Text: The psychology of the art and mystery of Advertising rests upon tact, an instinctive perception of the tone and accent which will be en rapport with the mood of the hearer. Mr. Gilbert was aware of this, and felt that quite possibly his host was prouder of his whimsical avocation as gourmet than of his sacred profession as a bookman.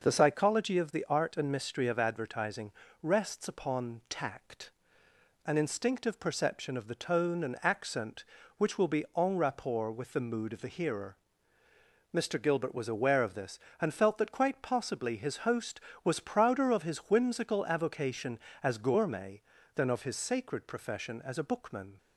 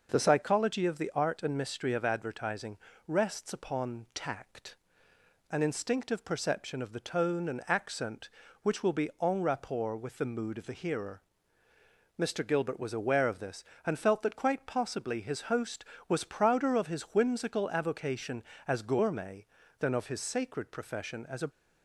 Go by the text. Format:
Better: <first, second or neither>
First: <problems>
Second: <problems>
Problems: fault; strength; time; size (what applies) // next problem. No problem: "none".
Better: first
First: pauses between "Advertising" and "rests"; slight; at 2.7 s; 0.30 s long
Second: pauses between "Advertising" and "rests"; slight; at 2.7 s; 0.29 s long // stops before "bookman"; at 21.5 s